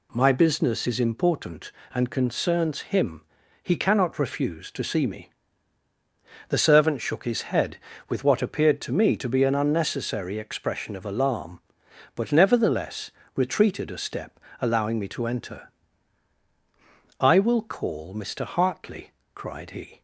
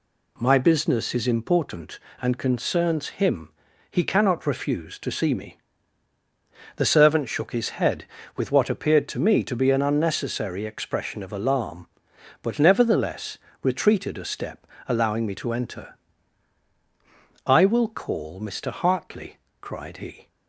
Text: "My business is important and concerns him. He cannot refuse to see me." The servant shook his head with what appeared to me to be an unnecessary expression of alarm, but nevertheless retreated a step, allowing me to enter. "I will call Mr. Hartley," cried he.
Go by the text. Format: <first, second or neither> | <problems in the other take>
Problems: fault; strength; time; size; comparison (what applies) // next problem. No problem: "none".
neither | pauses between "nevertheless" and "retreated"; slight; the same in both